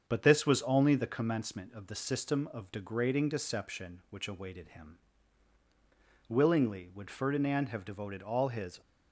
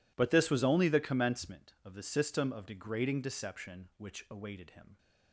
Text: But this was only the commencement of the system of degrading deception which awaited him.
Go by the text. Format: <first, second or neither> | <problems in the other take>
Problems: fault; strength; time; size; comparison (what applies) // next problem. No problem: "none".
second | starts louder than the rest; strong; until 1.0 s; 7 dB // goes on to say "Willingly would Ferdinand have devoted all his"; strong; from 6.2 s on; 2.5 s long